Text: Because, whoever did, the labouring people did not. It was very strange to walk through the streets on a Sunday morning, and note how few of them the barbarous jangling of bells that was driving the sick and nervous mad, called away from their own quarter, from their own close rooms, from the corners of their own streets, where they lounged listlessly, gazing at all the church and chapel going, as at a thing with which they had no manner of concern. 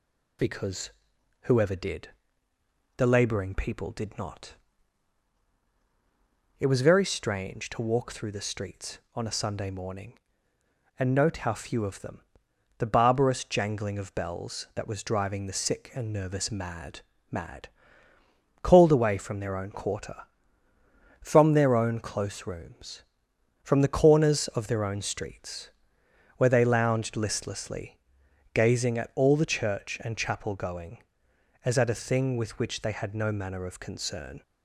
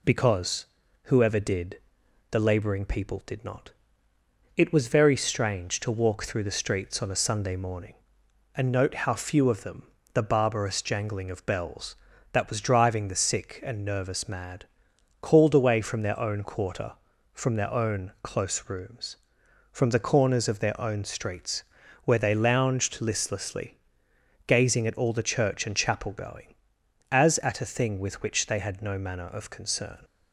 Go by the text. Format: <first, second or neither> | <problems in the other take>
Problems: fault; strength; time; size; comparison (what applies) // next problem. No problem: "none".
second | pauses between "them" and "the"; noticeable; at 12.2 s; 0.56 s long; slight in the second // says "mad" twice; at 17.2 s